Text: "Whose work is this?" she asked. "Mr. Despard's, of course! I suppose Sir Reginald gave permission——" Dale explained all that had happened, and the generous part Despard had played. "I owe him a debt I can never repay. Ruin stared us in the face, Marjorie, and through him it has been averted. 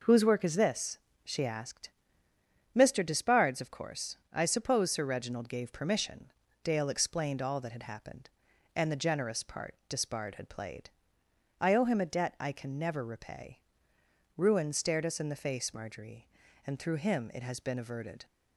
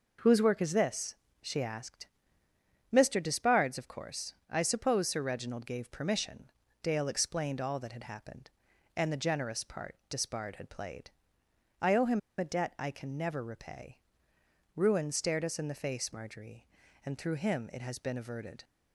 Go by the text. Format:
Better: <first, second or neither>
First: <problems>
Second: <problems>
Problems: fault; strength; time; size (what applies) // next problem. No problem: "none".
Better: first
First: none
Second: pauses between "him" and "a"; slight; at 12.1 s; 0.18 s long